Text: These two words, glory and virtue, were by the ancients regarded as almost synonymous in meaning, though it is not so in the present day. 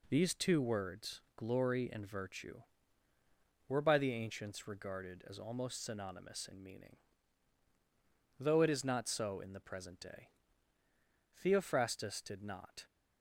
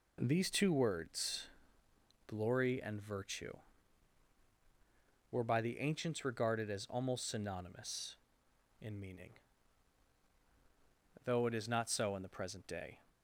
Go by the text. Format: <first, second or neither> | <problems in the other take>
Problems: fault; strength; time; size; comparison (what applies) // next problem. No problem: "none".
second | goes on to say "Theophrastus did not"; from 11.3 s on; 1.5 s long